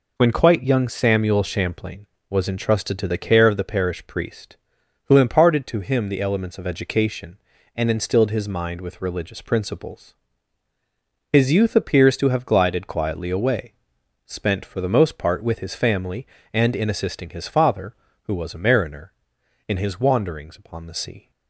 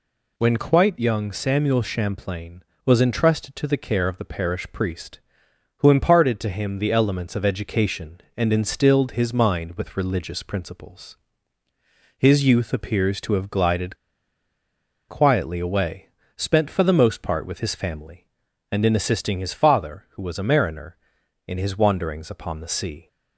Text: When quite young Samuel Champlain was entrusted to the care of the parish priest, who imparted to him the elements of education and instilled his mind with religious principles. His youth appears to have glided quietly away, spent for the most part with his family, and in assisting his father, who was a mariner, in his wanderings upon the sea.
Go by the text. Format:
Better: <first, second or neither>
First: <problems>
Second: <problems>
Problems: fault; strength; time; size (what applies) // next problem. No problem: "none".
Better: first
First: none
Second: pauses between "glided" and "quietly"; at 13.9 s; 1.1 s long